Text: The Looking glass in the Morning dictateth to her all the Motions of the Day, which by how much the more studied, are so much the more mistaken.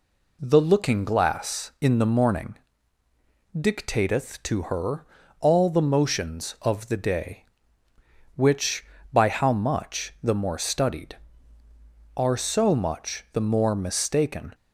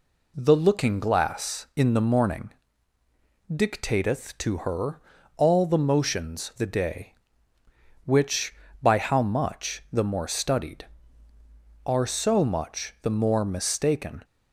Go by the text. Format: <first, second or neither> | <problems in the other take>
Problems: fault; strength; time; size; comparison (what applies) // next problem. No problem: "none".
first | pauses between "Morning" and "dictateth"; noticeable; at 2.5 s; 0.98 s long; noticeable in the first // pauses between "her" and "all"; at 4.9 s; 0.38 s long; also in the first // skips "of"; at 6.5 s